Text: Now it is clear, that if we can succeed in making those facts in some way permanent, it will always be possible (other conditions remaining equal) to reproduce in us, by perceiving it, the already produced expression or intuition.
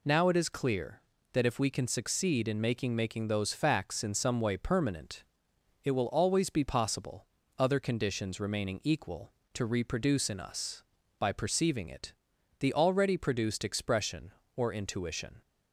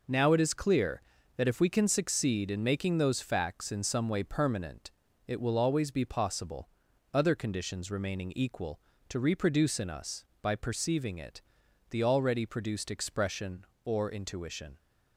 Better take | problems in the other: second | says "making" twice; at 2.9 s

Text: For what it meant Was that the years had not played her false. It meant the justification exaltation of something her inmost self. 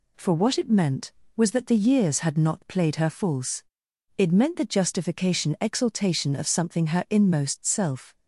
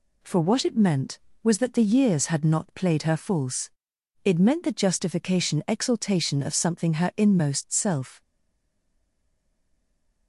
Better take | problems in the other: first | stays silent after the last word; noticeable; from 8.2 s on; 2.0 s long

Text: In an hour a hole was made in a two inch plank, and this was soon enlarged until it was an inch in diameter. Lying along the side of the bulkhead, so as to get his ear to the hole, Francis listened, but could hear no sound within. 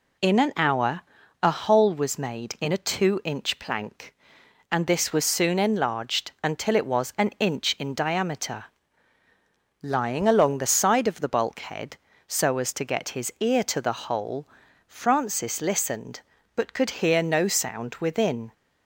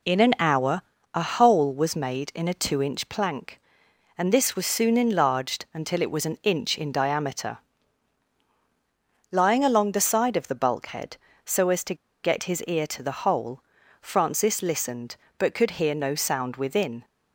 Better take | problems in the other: first | pauses between "hour" and "a"; slight; at 0.8 s; 0.32 s long; also in the first // pauses between "to" and "get"; slight; at 11.9 s; 0.28 s long

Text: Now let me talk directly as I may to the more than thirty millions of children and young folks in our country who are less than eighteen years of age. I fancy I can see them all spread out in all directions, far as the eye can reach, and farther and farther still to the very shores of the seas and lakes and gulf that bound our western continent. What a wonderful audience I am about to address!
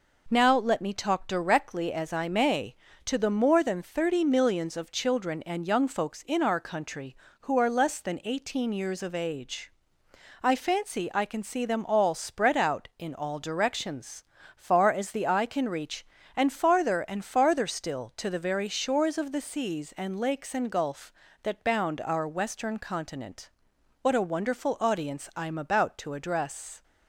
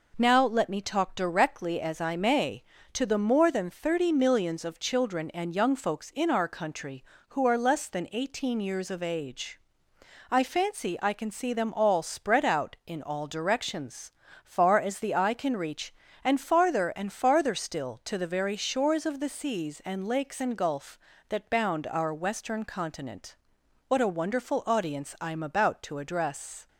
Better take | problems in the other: neither | none

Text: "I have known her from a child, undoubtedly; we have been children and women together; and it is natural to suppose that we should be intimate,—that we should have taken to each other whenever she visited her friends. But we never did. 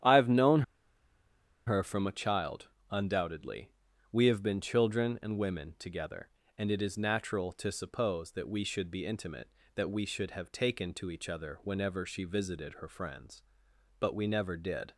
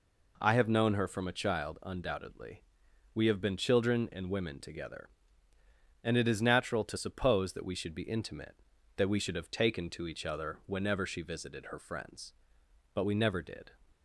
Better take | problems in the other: second | starts louder than the rest; strong; until 2.0 s; 10 dB // pauses between "known" and "her"; at 0.6 s; 1.0 s long

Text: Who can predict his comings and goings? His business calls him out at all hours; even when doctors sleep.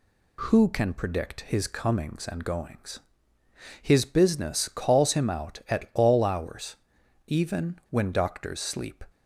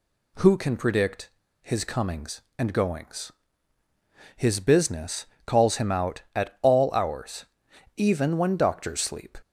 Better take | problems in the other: first | pauses between "predict" and "his"; slight; at 1.2 s; 0.32 s long // pauses between "business" and "calls"; slight; at 5.2 s; 0.20 s long

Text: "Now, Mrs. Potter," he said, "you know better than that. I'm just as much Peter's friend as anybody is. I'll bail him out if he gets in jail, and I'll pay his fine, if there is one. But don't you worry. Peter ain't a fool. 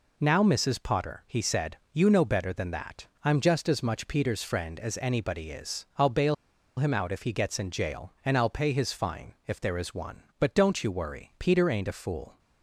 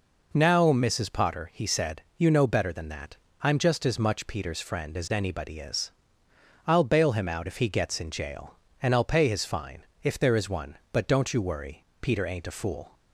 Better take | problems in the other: second | pauses between "bail" and "him"; at 6.3 s; 0.43 s long

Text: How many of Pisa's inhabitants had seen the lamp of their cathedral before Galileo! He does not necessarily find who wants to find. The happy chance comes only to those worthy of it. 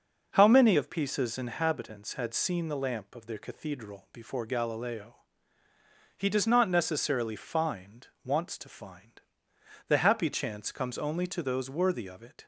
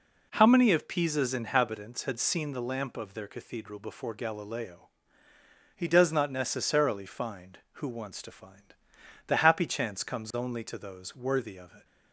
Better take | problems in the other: second | skips "who"; at 8.1 s

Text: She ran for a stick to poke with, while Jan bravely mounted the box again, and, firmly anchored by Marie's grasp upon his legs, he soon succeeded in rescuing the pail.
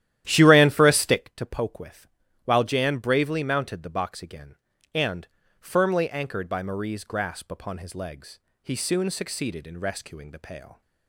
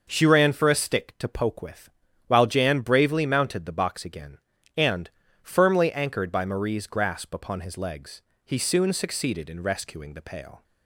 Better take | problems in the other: second | starts louder than the rest; strong; until 1.3 s; 12.5 dB

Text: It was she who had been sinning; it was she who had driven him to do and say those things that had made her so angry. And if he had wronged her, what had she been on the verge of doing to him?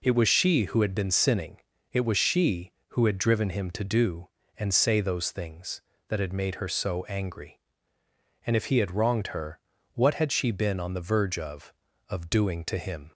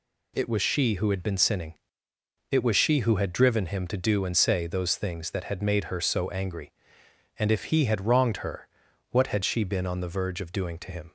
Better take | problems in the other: second | says "of" twice; at 12.0 s

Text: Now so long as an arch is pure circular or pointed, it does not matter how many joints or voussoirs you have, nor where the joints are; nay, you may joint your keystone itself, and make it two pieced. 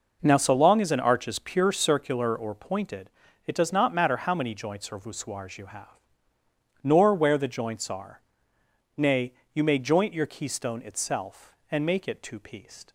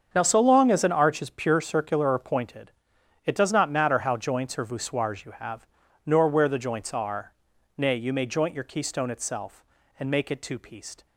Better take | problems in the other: first | starts louder than the rest; strong; until 1.1 s; 7.5 dB // skips "many"; at 4.1 s

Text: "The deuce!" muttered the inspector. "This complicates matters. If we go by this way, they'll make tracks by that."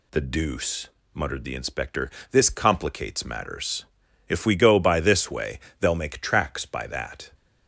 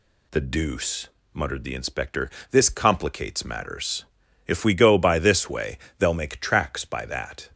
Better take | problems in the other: neither | none

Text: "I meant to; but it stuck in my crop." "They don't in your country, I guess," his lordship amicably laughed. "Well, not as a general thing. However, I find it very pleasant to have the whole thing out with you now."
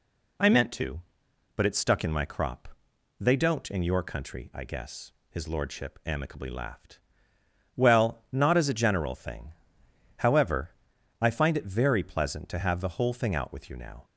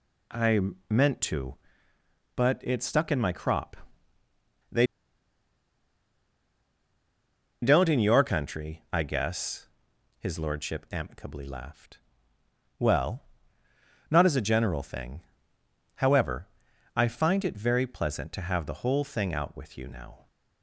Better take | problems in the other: first | pauses between "I" and "meant"; slight; at 0.5 s; 0.30 s long // pauses between "They" and "don't"; strong; at 4.8 s; 2.7 s long

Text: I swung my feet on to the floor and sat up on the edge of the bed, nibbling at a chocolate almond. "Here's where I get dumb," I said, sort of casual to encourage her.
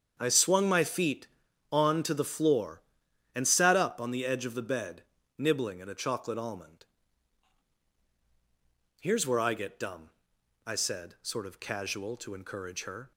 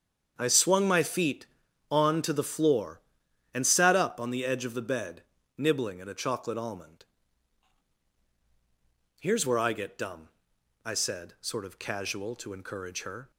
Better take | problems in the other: neither | starts louder than the rest; strong; the same in both

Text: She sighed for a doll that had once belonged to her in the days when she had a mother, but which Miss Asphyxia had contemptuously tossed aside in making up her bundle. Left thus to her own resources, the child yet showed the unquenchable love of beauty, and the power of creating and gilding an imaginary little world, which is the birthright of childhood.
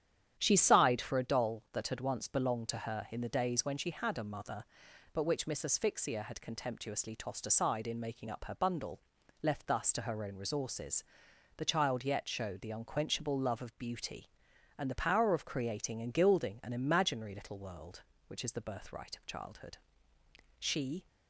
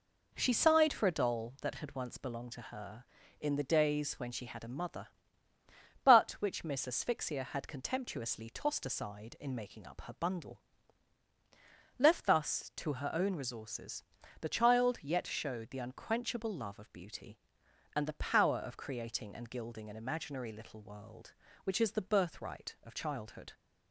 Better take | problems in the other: second | starts louder than the rest; strong; until 1.3 s; 10 dB // goes on to say "She"; slight; from 20.5 s on; 0.48 s long

